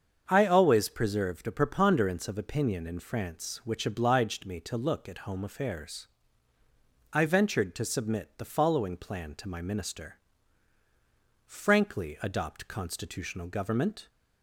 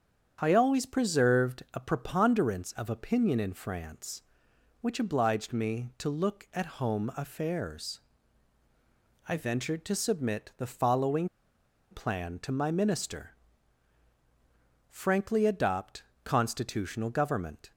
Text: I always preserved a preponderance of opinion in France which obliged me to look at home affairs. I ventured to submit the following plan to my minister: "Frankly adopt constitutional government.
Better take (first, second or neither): first